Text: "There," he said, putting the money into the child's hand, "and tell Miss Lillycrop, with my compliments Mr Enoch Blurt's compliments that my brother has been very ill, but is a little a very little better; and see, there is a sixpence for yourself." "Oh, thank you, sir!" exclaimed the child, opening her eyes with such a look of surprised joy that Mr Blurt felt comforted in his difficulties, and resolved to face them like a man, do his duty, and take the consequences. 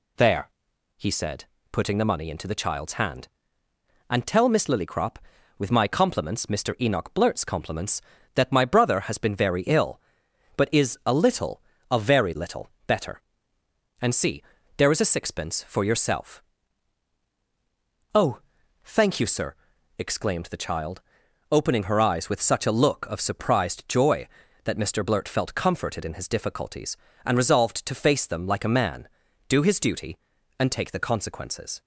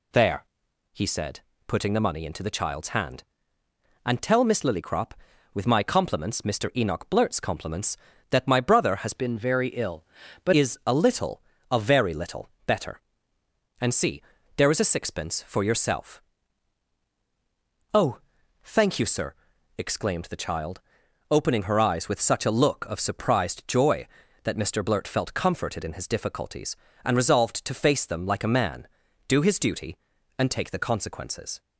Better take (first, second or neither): first